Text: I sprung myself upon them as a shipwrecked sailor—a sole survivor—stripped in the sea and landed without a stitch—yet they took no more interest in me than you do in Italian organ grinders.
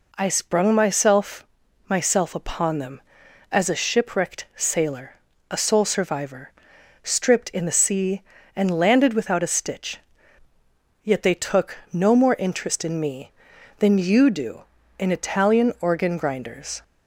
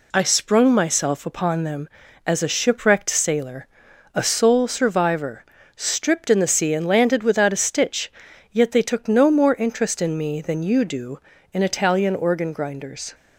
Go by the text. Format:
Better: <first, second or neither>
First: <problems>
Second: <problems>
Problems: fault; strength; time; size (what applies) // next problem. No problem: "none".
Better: second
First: says "myself" twice; at 1.8 s // pauses between "took" and "no"; slight; at 11.7 s; 0.16 s long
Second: none